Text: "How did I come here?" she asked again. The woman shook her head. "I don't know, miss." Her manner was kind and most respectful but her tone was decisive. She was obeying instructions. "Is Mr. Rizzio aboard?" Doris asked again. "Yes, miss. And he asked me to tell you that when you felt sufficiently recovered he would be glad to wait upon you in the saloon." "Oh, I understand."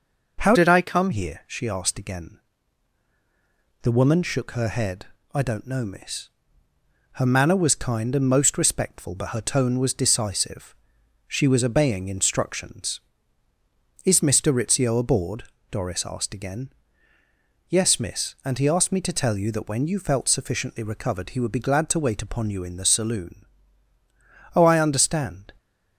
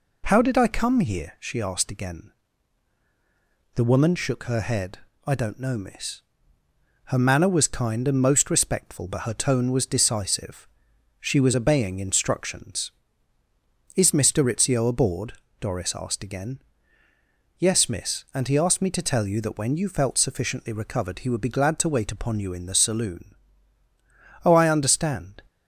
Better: second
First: changes voice from "did" to "come"; from 0.5 to 1.0 s; 0.5 s long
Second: none

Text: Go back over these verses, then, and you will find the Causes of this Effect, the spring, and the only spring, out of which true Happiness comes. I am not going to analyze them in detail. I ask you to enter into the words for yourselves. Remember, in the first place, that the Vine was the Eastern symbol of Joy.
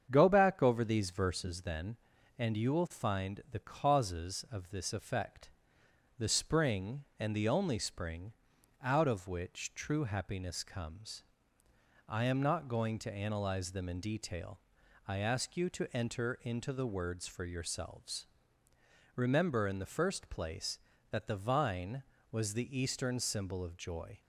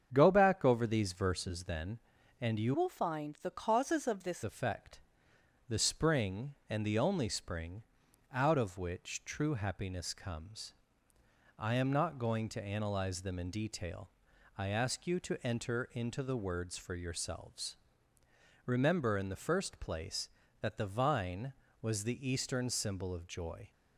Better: first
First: starts louder than the rest; strong; until 1.1 s; 7.5 dB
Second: starts louder than the rest; strong; until 1.1 s; 7.5 dB // changes voice from "will" to "this"; from 2.7 to 4.4 s; 1.7 s long

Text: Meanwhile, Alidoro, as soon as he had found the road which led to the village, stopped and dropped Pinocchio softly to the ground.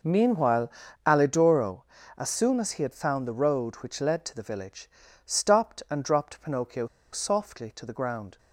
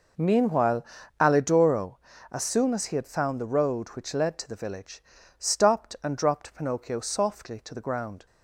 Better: second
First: pauses between "Pinocchio" and "softly"; slight; at 6.8 s; 0.25 s long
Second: none

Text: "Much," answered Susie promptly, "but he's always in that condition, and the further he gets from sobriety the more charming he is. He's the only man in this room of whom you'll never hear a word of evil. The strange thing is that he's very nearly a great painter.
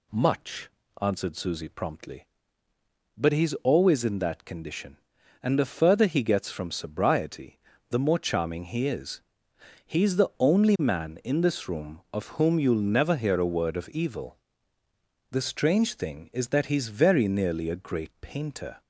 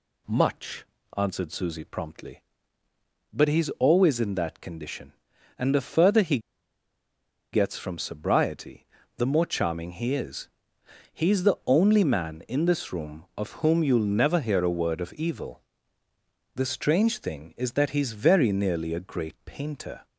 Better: first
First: pauses between "sobriety" and "the"; slight; at 7.5 s; 0.32 s long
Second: pauses between "he" and "gets"; at 6.3 s; 1.1 s long // pauses between "sobriety" and "the"; slight; at 8.8 s; 0.32 s long

